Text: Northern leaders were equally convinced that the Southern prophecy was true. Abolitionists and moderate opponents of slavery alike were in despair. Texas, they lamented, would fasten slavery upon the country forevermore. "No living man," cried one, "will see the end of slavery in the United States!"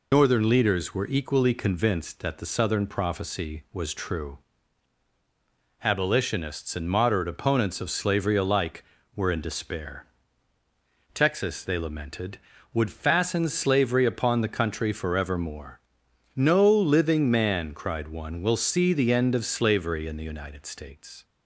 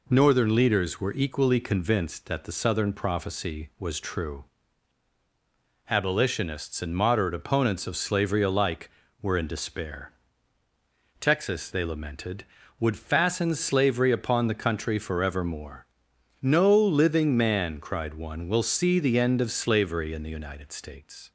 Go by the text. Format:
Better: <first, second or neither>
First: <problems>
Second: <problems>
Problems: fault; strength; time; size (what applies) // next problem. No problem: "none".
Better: second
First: loses the start of "Northern"; at 0.1 s; 115 ms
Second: none